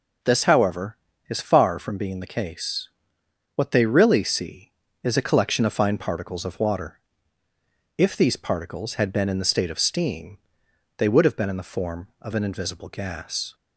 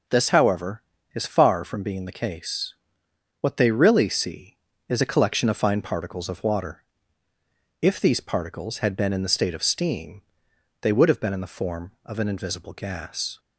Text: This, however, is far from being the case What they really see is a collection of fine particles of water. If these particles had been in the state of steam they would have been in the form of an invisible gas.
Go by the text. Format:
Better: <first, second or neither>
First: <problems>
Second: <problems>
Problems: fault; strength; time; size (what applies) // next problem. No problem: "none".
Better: neither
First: pauses between "case" and "What"; noticeable; at 2.8 s; 0.66 s long // pauses between "steam" and "they"; noticeable; at 10.3 s; 0.60 s long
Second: pauses between "case" and "What"; noticeable; at 2.7 s; 0.66 s long // pauses between "steam" and "they"; noticeable; at 10.2 s; 0.60 s long